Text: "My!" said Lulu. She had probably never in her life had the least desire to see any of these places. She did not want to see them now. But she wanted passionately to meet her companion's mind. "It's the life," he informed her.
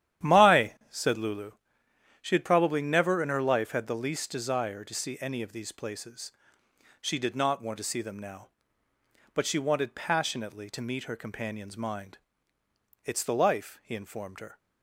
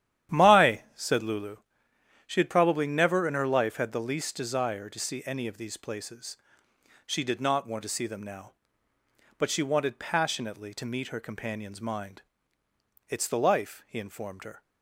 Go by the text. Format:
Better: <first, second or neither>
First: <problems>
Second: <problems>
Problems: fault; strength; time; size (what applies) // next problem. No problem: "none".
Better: neither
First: starts louder than the rest; strong; until 1.3 s; 11 dB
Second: starts louder than the rest; strong; until 1.4 s; 11 dB